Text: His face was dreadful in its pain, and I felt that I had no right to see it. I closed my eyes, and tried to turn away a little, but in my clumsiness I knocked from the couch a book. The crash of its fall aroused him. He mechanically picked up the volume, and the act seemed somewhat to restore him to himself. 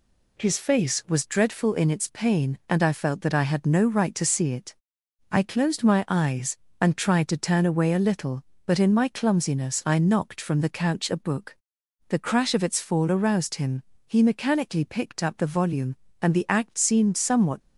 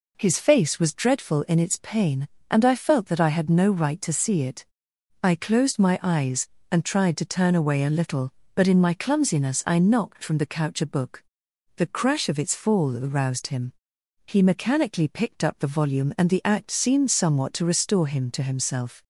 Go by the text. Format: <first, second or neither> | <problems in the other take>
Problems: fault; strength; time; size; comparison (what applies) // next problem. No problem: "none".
second | stops before "to restore him to himself"; at 17.6 s